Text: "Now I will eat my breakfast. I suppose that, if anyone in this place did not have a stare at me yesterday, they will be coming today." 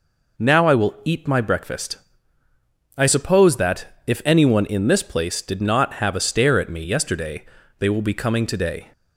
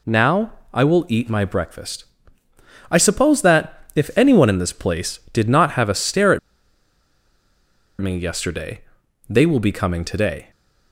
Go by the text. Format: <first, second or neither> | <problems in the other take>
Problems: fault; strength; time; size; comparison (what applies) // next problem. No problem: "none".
first | pauses between "Now" and "I"; slight; at 0.5 s; 0.20 s long // pauses between "at" and "me"; strong; at 6.3 s; 1.6 s long